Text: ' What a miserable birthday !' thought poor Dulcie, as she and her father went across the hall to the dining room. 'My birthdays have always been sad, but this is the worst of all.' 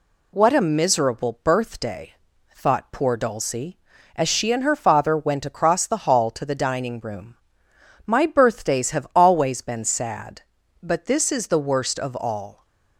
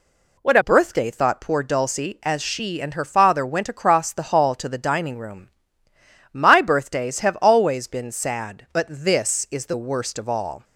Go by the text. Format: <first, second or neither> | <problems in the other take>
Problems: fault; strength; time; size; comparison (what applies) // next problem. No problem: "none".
first | skips "miserable"; at 0.6 s